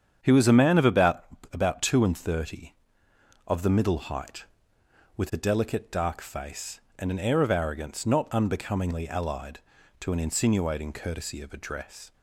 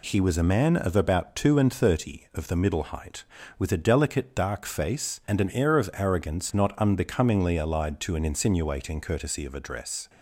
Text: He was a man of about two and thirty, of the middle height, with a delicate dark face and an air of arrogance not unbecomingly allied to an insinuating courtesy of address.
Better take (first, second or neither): second